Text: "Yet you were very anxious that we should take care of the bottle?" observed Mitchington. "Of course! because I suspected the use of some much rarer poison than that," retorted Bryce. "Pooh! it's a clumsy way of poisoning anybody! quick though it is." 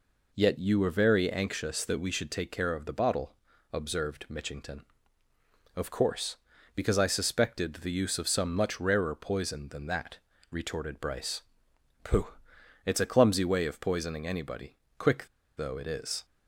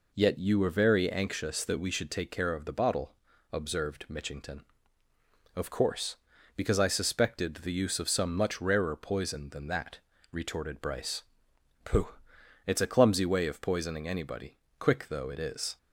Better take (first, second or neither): second